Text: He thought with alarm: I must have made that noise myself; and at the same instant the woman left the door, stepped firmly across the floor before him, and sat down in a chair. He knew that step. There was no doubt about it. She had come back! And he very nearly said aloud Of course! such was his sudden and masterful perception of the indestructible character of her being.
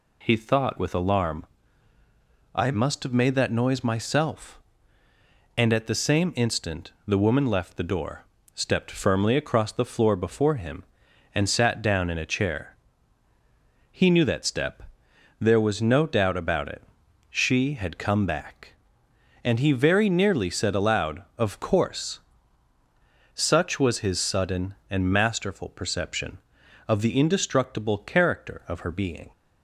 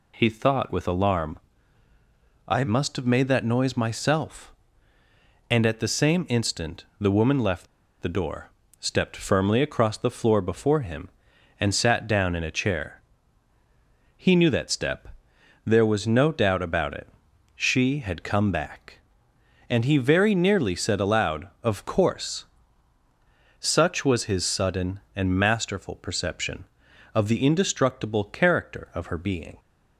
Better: first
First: pauses between "instant" and "the"; slight; at 6.9 s; 0.16 s long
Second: pauses between "instant" and "the"; slight; at 6.8 s; 0.16 s long // pauses between "left" and "the"; slight; at 7.6 s; 0.33 s long

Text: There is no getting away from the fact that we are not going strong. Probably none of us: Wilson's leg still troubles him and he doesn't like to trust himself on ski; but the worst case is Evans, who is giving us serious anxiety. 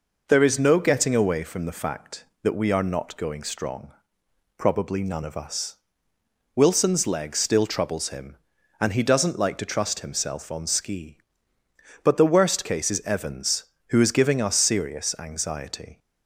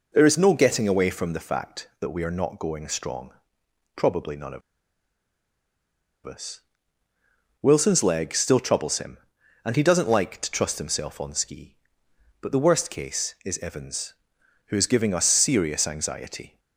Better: first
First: none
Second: pauses between "of" and "us"; strong; at 4.6 s; 1.6 s long

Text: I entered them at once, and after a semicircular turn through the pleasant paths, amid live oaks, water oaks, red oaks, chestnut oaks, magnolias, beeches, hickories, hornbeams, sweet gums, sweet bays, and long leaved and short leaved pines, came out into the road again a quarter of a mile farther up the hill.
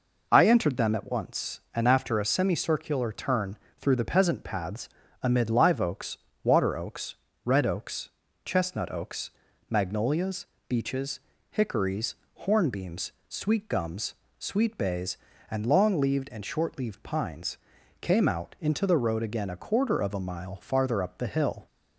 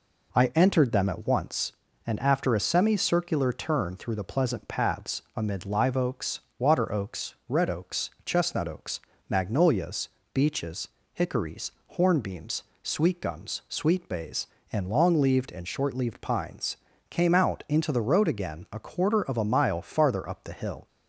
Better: second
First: pauses between "turn" and "through"; slight; at 3.5 s; 0.22 s long // says "peasant" for "pleasant"; at 4.0 s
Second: none

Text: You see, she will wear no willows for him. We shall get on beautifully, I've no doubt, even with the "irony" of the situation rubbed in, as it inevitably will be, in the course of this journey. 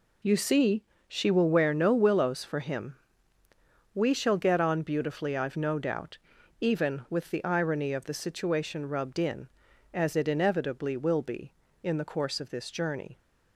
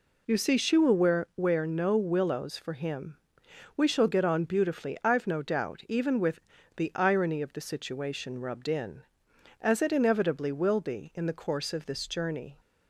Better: first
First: none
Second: says "wear" twice; at 1.3 s // pauses between "with" and "the"; at 6.4 s; 0.36 s long

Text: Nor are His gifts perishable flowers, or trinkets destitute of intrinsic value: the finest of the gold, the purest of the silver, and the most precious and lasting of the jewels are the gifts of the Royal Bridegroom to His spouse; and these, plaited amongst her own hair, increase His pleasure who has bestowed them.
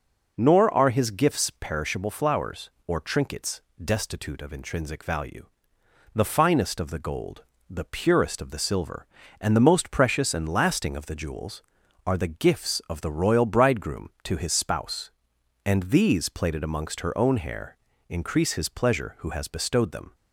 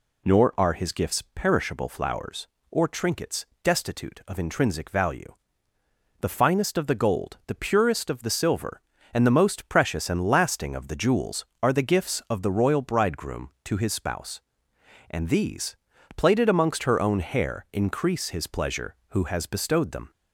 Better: neither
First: pauses between "trinkets" and "destitute"; slight; at 3.6 s; 0.22 s long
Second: pauses between "trinkets" and "destitute"; slight; at 3.4 s; 0.18 s long

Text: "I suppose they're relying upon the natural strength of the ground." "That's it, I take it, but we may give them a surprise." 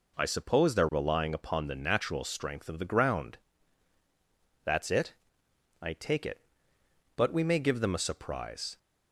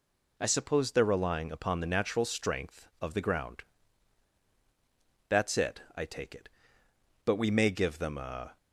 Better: first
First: none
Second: stops before "surprise"; at 8.5 s

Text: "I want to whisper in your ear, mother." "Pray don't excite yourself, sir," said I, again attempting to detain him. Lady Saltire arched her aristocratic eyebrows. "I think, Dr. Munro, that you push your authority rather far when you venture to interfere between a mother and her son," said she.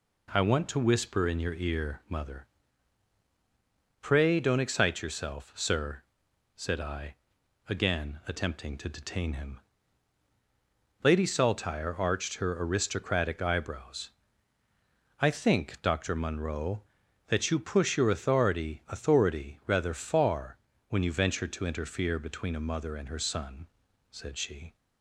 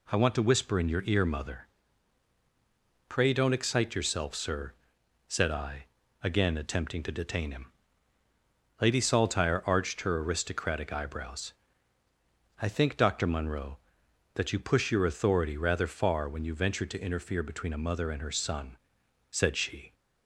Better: second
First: says "authority" twice; at 18.8 s // pauses between "far" and "when"; slight; at 20.5 s; 0.30 s long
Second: none

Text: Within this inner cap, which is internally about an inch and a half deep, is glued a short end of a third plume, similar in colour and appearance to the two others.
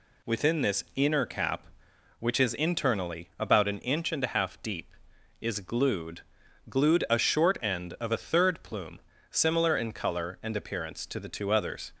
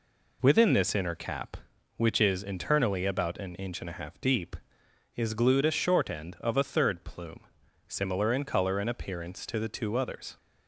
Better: second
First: says "glued" twice; at 6.6 s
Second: none

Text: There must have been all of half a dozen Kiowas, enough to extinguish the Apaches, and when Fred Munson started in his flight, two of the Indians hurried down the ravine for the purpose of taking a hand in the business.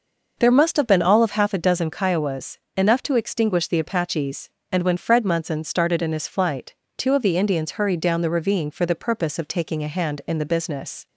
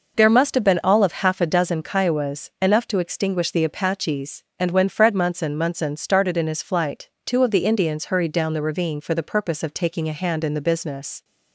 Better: first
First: none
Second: says "Munson" twice; at 5.5 s

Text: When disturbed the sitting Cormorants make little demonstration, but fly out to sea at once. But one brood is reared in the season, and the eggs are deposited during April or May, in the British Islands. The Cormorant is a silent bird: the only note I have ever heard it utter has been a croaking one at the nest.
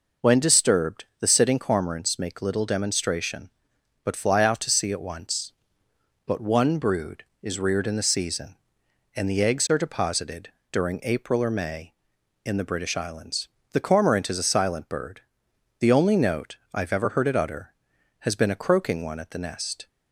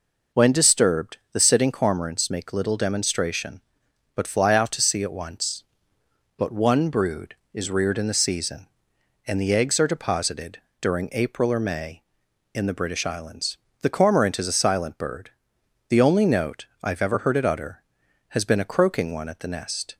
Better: neither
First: pauses between "deposited" and "during"; slight; at 10.4 s; 0.22 s long // pauses between "note" and "I"; slight; at 16.5 s; 0.18 s long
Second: pauses between "deposited" and "during"; slight; at 10.5 s; 0.22 s long // pauses between "note" and "I"; slight; at 16.6 s; 0.18 s long

